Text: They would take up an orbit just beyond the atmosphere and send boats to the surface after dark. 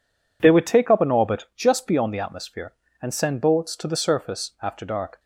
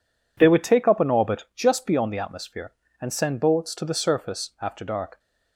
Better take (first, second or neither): neither